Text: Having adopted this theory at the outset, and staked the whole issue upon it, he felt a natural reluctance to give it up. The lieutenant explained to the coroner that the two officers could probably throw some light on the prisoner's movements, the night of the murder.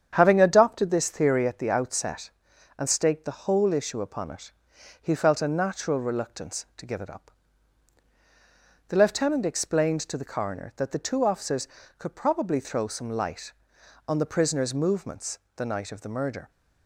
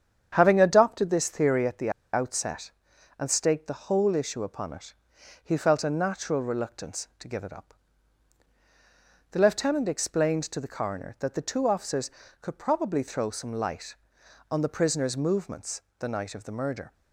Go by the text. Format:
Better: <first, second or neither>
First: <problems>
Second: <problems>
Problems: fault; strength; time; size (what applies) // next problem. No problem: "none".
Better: first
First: starts louder than the rest; strong; until 1.1 s; 8.5 dB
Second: starts louder than the rest; strong; until 1.3 s; 8.5 dB // pauses between "the" and "outset"; slight; at 1.9 s; 0.22 s long